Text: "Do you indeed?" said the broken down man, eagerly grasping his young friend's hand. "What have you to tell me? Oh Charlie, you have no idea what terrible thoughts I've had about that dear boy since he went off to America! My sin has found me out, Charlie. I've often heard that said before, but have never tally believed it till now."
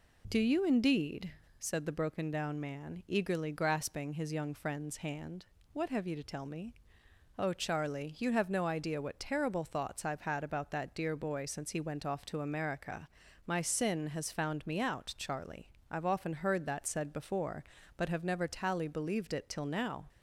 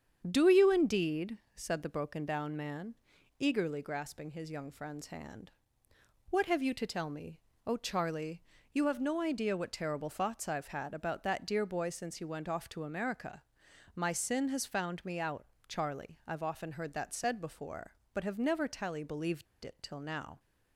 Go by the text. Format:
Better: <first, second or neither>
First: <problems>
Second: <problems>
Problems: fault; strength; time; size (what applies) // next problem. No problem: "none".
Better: first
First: none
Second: starts louder than the rest; strong; until 1.2 s; 8 dB // pauses between "believed" and "it"; slight; at 19.4 s; 0.19 s long